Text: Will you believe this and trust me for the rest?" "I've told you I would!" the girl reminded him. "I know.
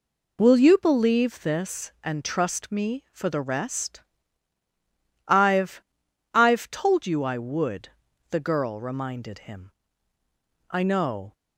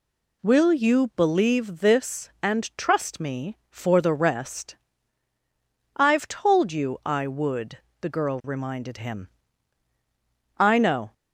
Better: second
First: says "I've" twice; at 6.3 s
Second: none

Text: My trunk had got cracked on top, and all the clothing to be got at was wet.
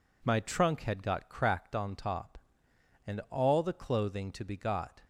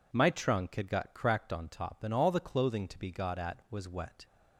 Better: second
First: stops before "at was wet"; at 5.0 s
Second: none

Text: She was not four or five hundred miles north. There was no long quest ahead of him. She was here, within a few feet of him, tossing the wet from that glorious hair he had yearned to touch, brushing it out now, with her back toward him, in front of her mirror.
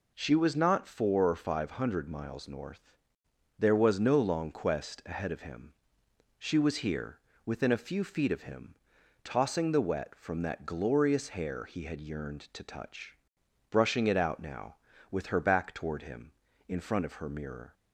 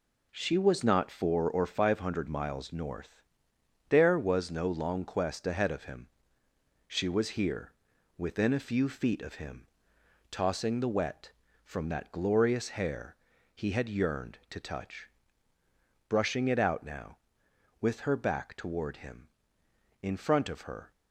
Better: first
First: none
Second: pauses between "hair" and "he"; at 13.1 s; 0.40 s long // stops before "mirror"; at 20.9 s

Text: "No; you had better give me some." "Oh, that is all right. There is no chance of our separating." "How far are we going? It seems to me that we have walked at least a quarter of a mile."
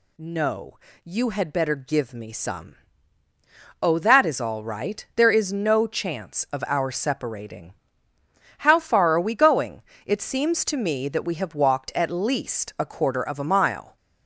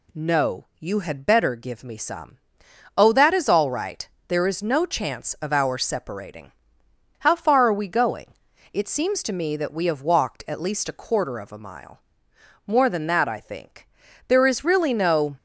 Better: first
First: none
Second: goes on to say "More than that I think There is really no"; strong; from 12.6 s on; 2.7 s long

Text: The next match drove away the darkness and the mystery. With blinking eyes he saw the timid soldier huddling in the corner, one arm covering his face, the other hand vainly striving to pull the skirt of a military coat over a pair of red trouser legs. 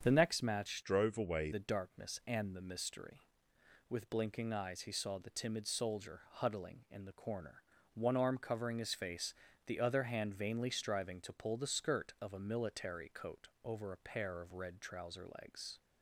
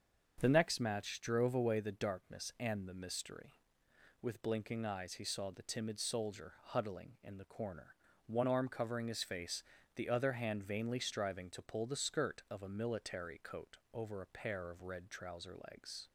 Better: second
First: starts louder than the rest; strong; until 1.0 s; 7 dB // changes voice from "drove" to "away"; from 0.8 to 1.5 s; 0.7 s long // pauses between "coat" and "over"; slight; at 13.4 s; 0.16 s long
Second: starts louder than the rest; until 1.3 s; 6.5 dB // pauses between "coat" and "over"; slight; at 13.7 s; 0.16 s long

